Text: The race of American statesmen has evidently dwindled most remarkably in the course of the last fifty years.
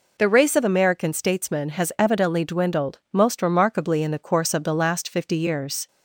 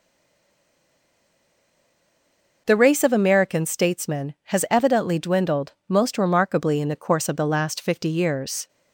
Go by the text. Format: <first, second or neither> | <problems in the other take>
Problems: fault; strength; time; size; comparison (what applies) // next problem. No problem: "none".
first | stays silent before the first word; strong; until 2.6 s; 2.6 s long // pauses between "dwindled" and "most"; slight; at 5.7 s; 0.16 s long